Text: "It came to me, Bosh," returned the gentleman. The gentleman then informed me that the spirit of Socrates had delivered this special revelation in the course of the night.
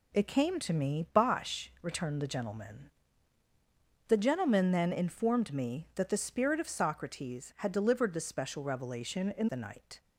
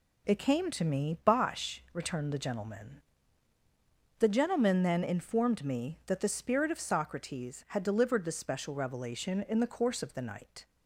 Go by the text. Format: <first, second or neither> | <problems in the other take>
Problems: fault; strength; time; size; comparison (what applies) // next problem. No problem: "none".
second | skips "the course of"; at 9.4 s